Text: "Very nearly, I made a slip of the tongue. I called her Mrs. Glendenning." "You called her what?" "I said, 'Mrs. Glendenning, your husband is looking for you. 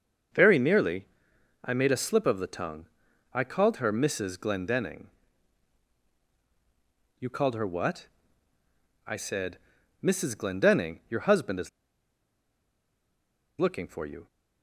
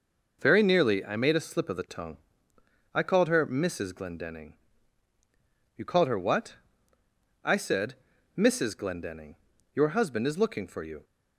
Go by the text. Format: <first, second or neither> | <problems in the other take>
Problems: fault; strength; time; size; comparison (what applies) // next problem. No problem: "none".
second | starts louder than the rest; until 1.9 s; 6.5 dB // pauses between "is" and "looking"; strong; at 11.6 s; 1.8 s long